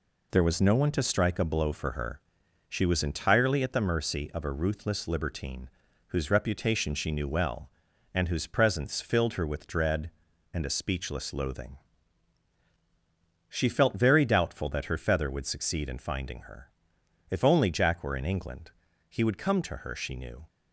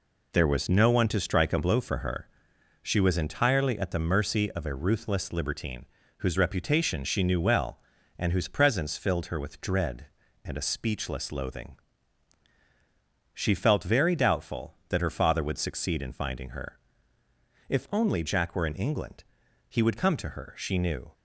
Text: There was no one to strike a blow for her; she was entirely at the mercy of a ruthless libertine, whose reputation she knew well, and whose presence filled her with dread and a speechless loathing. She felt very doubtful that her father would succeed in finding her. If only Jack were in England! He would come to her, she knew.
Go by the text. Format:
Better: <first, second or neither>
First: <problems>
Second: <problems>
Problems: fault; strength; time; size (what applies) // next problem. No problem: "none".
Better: second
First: says "feather" for "father"; at 14.9 s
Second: none